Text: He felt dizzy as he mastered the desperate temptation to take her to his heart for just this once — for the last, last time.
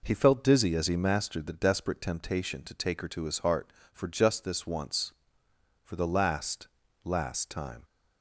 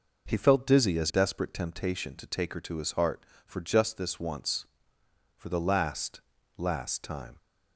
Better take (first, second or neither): first